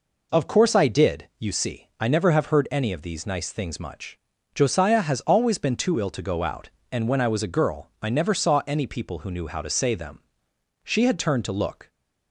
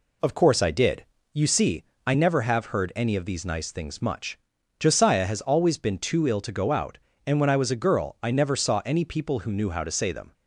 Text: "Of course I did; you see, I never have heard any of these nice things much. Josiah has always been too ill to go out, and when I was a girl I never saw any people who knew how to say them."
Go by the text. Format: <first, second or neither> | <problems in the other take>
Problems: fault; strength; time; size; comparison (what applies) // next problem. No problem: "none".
second | goes on to say "She had turned to look"; noticeable; from 10.8 s on; 1.0 s long